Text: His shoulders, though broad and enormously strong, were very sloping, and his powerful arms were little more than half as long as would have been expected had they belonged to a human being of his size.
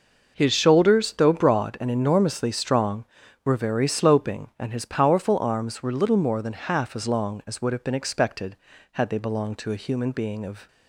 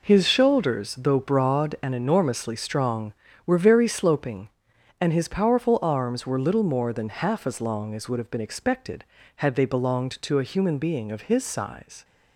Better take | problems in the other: second | stops before "his size"; at 10.6 s

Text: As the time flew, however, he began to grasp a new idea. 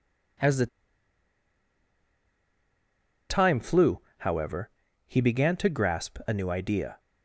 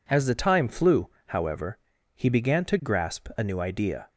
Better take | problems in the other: second | pauses between "the" and "time"; strong; at 0.6 s; 2.6 s long

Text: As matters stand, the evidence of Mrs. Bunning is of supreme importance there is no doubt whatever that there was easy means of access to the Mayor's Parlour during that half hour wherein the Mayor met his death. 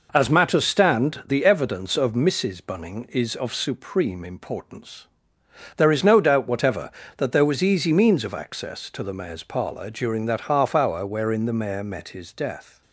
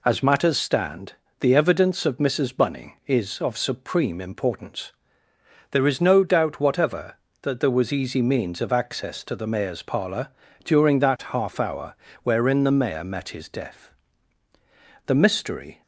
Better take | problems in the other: first | pauses between "importance" and "there"; noticeable; at 4.9 s; 0.80 s long; noticeable in the first // pauses between "Parlour" and "during"; slight; at 10.2 s; 0.34 s long // pauses between "hour" and "wherein"; slight; at 11.9 s; 0.28 s long // goes on to say "The mystery"; noticeable; from 15.0 s on; 0.76 s long

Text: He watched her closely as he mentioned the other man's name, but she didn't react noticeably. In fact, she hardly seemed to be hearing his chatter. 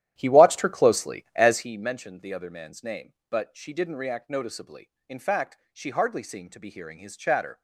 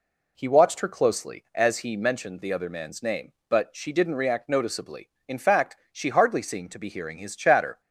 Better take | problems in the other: second | starts louder than the rest; strong; until 1.7 s; 11.5 dB

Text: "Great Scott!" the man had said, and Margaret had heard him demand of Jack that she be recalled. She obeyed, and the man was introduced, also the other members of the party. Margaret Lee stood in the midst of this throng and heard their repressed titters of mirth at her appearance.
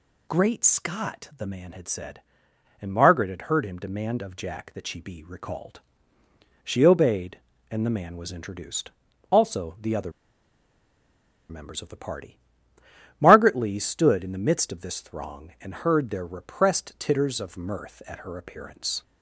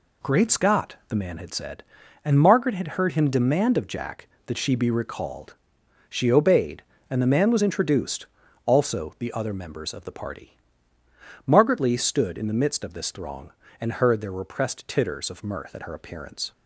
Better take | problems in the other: second | pauses between "other" and "members"; strong; at 10.1 s; 1.3 s long

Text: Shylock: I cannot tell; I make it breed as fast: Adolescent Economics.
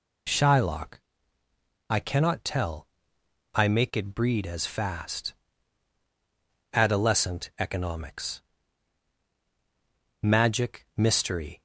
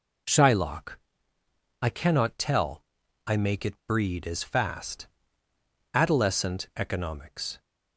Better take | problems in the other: second | goes on to say "Magic Mystery"; from 10.2 s on; 1.4 s long

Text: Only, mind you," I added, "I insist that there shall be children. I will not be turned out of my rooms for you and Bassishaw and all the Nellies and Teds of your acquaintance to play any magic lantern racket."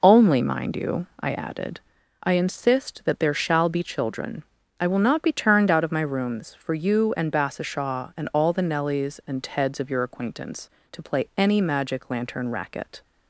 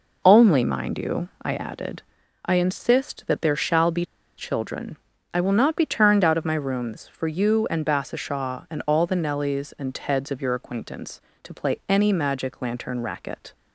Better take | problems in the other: first | pauses between "be" and "children"; slight; at 4.0 s; 0.32 s long

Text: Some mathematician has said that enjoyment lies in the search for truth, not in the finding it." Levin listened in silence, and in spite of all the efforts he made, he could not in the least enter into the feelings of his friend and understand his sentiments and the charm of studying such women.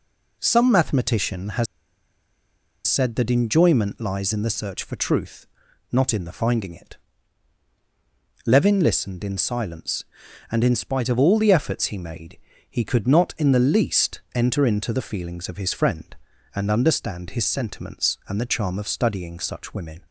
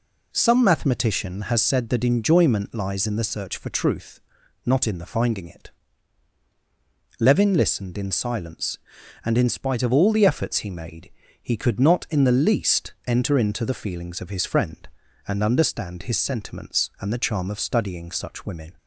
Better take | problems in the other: second | pauses between "has" and "said"; at 1.6 s; 1.2 s long // pauses between "least" and "enter"; slight; at 14.1 s; 0.16 s long; slight in the second

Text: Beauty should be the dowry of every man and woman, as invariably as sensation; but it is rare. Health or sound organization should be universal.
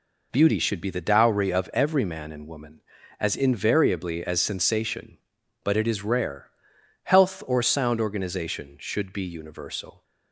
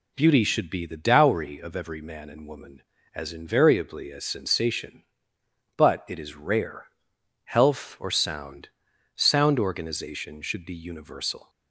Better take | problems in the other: first | says "sound" twice; at 9.1 s

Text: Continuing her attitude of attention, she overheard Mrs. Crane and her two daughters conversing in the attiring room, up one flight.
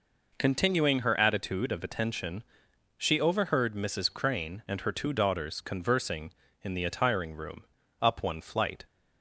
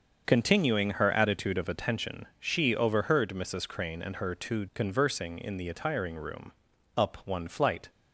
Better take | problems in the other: first | starts louder than the rest; until 1.2 s; 6.5 dB // skips "daughters"; at 4.6 s

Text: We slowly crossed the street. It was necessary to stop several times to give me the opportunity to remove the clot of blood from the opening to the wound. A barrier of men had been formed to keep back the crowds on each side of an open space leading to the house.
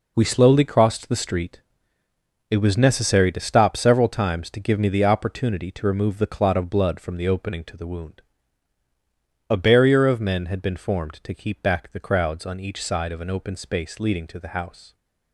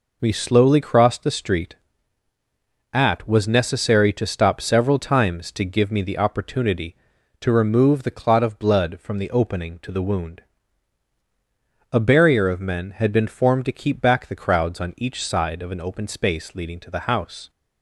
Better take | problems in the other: first | says "At" for "It"; at 2.9 s

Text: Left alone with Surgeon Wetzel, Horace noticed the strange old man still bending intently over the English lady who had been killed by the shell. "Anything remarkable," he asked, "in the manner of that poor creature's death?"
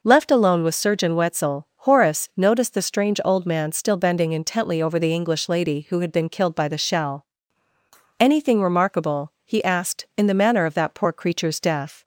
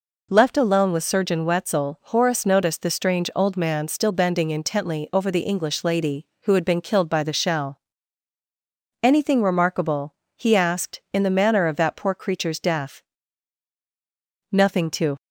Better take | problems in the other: first | goes on to say "Nothing to"; noticeable; from 14.5 s on; 0.66 s long

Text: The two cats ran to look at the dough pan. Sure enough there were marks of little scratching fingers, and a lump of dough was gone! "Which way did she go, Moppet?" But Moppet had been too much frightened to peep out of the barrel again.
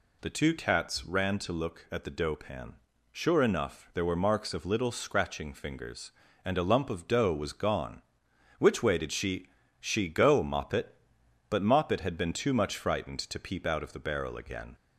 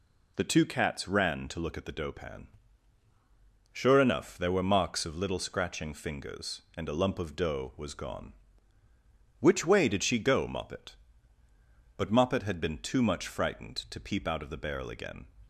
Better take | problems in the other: second | says "she" twice; at 9.7 s

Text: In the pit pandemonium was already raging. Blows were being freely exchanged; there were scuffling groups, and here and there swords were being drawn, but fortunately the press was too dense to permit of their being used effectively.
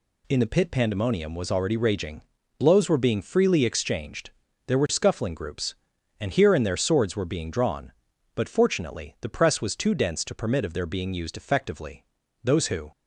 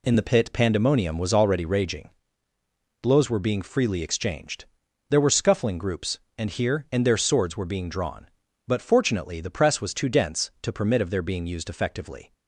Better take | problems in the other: second | goes on to say "Those who"; slight; from 12.4 s on; 0.48 s long

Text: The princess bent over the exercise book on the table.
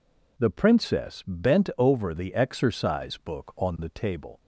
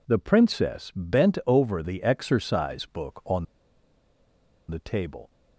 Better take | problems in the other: first | pauses between "on" and "the"; strong; at 3.4 s; 1.2 s long

